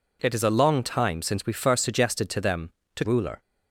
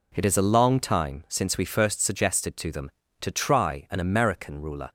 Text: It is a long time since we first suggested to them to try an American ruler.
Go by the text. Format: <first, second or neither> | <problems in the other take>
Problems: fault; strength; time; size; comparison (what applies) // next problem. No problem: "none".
second | skips "try an American"; at 3.0 s